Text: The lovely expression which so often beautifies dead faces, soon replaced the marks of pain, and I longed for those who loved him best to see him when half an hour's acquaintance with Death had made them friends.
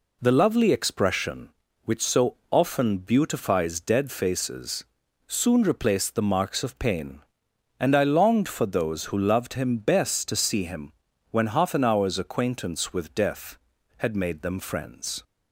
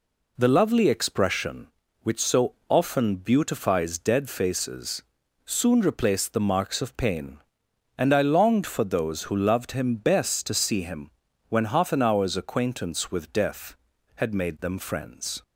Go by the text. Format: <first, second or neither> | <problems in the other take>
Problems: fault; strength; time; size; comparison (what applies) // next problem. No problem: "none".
neither | pauses between "him" and "when"; the same in both